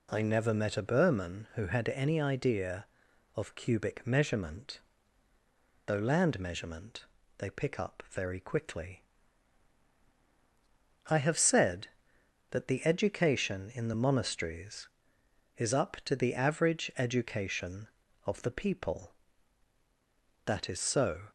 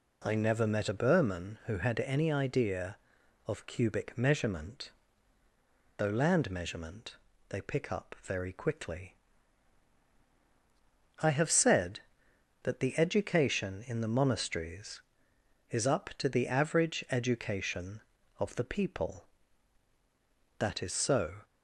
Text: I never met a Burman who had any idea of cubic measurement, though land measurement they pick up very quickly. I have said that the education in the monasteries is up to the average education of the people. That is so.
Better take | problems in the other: neither | pauses between "measurement" and "they"; slight; the same in both

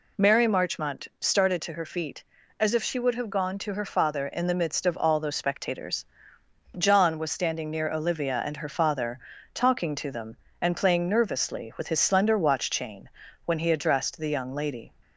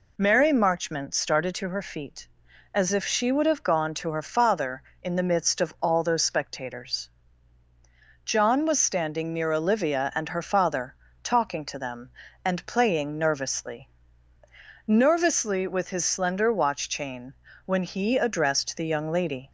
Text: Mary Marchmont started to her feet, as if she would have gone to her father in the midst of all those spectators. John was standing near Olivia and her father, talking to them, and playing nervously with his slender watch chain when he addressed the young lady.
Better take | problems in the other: first | says "nervously" twice; at 14.8 s // pauses between "chain" and "when"; slight; at 17.3 s; 0.32 s long; slight in the first

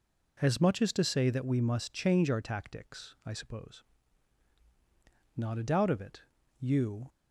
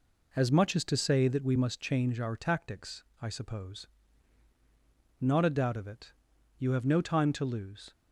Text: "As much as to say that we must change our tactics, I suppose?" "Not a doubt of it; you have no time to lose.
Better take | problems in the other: second | stops before "have no time to lose"; at 7.0 s

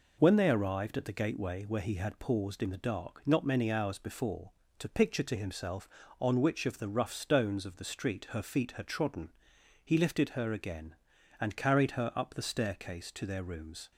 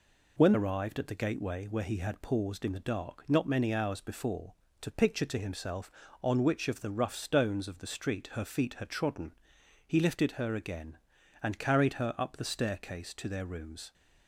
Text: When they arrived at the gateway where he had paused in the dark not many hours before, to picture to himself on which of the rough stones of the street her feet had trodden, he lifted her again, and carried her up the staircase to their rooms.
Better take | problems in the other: first | skips "they"; at 0.5 s

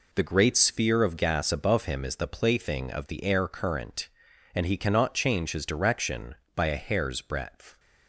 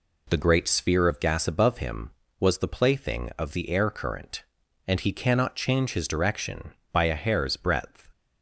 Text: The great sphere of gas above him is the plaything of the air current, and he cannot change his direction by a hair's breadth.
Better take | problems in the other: first | says "was" for "is"; at 2.4 s

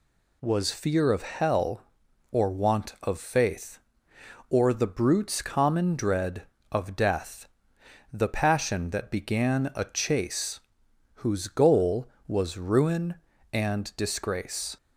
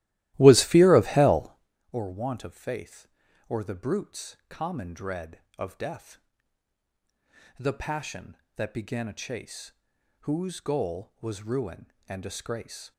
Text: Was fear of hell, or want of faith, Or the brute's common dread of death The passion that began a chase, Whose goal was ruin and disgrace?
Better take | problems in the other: first | starts louder than the rest; strong; until 1.8 s; 15.5 dB // pauses between "death" and "The"; strong; at 6.1 s; 1.4 s long; noticeable in the first

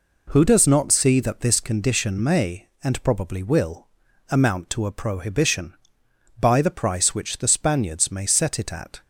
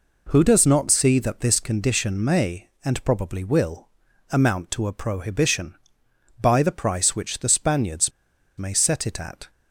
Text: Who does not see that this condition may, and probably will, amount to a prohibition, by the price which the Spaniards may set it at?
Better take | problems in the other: first | pauses between "Spaniards" and "may"; noticeable; at 8.1 s; 0.46 s long

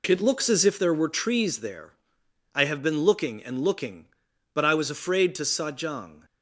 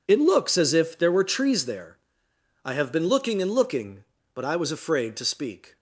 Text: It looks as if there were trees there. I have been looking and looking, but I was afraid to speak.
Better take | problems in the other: second | says "sajang" for "speak"; at 5.4 s

